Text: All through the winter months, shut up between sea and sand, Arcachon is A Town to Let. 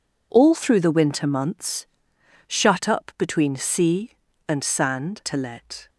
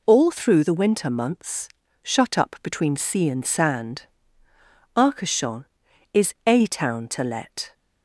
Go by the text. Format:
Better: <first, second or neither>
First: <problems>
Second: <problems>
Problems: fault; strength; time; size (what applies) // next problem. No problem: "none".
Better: second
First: skips "Arcachon is A Town"; at 5.2 s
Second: none